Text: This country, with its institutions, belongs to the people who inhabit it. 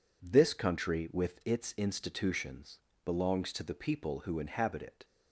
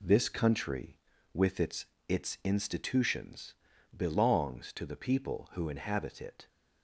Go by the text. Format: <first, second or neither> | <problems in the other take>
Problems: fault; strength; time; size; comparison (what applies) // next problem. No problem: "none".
first | says "its" twice; at 2.0 s